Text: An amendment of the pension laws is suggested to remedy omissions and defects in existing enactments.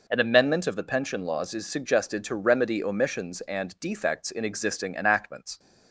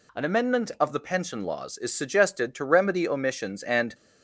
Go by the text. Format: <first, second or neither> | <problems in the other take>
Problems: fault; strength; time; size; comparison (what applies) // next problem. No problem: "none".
first | stops before "defects in existing enactments"; at 3.9 s